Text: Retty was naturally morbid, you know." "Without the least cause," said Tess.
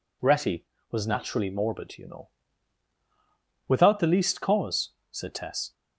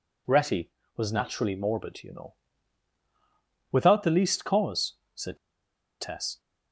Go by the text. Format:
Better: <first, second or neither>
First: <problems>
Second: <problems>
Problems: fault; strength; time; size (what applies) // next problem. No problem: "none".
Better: first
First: none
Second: pauses between "said" and "Tess"; noticeable; at 5.3 s; 0.64 s long